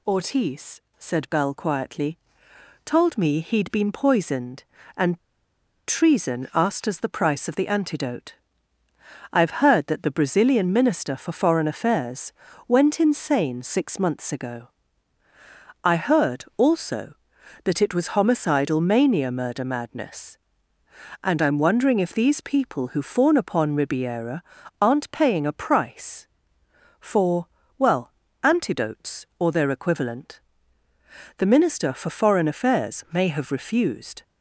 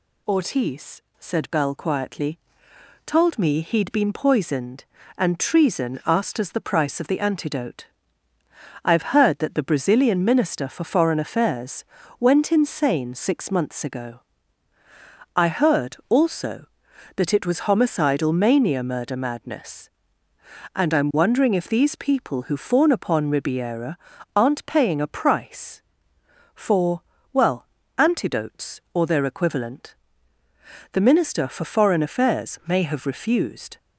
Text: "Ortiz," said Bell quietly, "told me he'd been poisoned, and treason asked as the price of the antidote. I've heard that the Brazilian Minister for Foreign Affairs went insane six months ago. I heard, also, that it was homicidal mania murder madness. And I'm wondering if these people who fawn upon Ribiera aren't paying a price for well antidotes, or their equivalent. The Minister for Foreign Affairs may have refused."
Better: second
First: pauses between "and" and "treason"; noticeable; at 5.1 s; 0.69 s long // pauses between "Affairs" and "went"; at 12.3 s; 0.38 s long // pauses between "Ribiera" and "aren't"; at 24.4 s; 0.38 s long // pauses between "for" and "well"; slight; at 27.4 s; 0.30 s long // pauses between "well" and "antidotes"; slight; at 28.1 s; 0.30 s long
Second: pauses between "Affairs" and "went"; at 11.8 s; 0.38 s long // pauses between "Ribiera" and "aren't"; at 23.9 s; 0.38 s long // pauses between "for" and "well"; slight; at 27.0 s; 0.30 s long // pauses between "well" and "antidotes"; slight; at 27.6 s; 0.30 s long

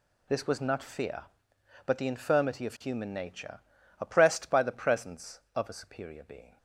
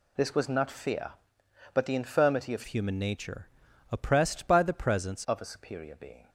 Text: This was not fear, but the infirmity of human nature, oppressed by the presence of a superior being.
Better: first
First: none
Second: changes voice from "human" to "presence"; from 2.6 to 5.2 s; 2.6 s long

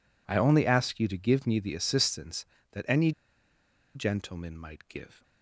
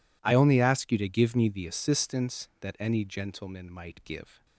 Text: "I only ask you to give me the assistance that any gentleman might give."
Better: second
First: pauses between "any" and "gentleman"; noticeable; at 3.1 s; 0.83 s long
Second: none

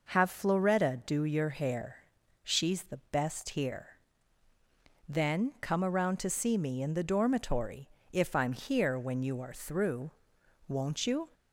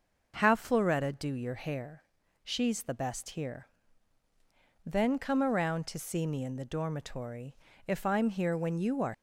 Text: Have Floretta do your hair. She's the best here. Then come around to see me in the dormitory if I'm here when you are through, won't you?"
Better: first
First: pauses between "dormitory" and "if"; slight; at 7.8 s; 0.24 s long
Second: pauses between "dormitory" and "if"; slight; at 7.5 s; 0.32 s long // stops before "through won't you"; at 9.1 s

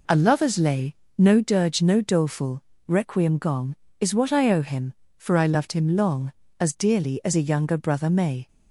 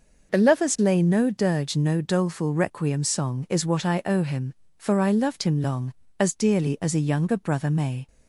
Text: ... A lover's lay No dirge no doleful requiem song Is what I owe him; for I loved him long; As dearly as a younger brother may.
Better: second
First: pauses between "lay" and "No"; slight; at 0.9 s; 0.24 s long // pauses between "doleful" and "requiem"; slight; at 2.6 s; 0.24 s long // says "gong" for "song"; at 3.3 s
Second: none

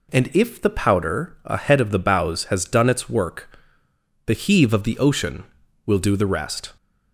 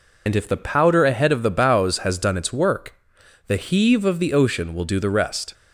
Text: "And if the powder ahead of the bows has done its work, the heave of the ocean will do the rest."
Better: first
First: none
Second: loses the start of "And"; at 0.2 s; 60 ms

